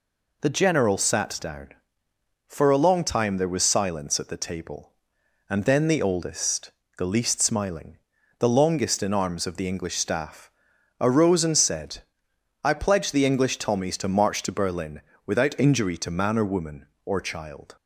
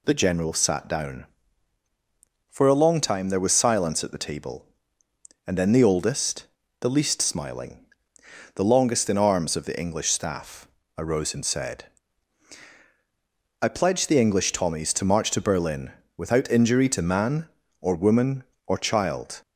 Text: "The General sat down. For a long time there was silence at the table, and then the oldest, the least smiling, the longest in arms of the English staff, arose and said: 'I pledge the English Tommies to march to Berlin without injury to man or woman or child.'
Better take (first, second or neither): neither